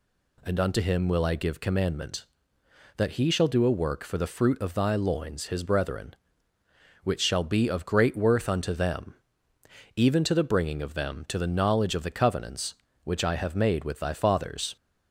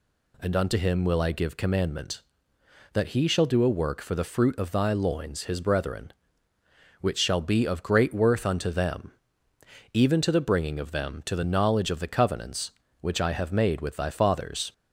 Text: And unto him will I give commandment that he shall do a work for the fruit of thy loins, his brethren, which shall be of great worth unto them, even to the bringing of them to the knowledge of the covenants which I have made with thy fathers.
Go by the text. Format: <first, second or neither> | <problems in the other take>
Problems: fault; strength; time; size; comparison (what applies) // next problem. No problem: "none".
neither | none